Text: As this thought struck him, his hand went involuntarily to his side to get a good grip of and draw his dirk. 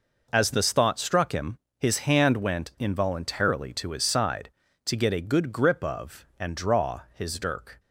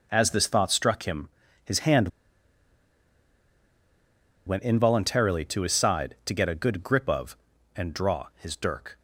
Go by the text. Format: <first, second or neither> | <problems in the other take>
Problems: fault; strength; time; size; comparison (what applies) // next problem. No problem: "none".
first | pauses between "hand" and "went"; strong; at 2.0 s; 2.3 s long